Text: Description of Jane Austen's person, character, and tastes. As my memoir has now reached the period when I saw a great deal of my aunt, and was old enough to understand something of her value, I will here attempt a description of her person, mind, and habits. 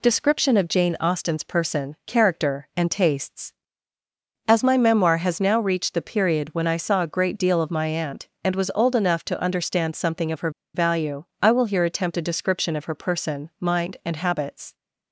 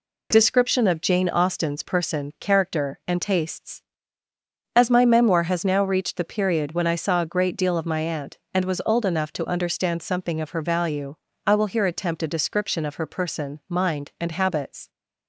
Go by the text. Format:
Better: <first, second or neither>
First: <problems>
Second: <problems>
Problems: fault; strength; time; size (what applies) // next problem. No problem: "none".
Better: second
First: pauses between "her" and "value"; slight; at 10.5 s; 0.24 s long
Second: none